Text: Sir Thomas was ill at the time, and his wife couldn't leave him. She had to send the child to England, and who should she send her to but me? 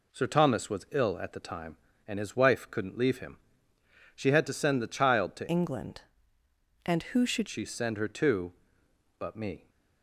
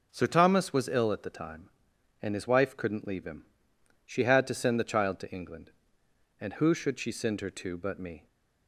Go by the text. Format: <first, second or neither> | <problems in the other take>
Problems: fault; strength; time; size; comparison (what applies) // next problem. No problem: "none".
second | changes voice from "England" to "should"; from 5.4 to 7.4 s; 2.0 s long